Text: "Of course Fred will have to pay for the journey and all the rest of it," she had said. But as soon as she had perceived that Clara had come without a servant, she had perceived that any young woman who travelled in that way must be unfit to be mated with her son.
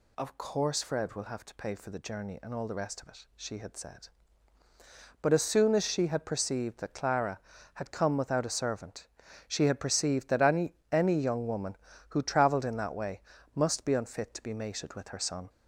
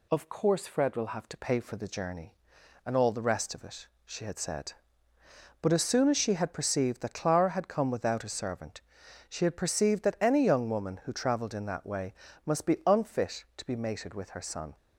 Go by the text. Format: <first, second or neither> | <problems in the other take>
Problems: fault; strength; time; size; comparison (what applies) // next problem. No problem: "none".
second | says "any" twice; at 10.9 s // pauses between "way" and "must"; slight; at 13.2 s; 0.34 s long; slight in the second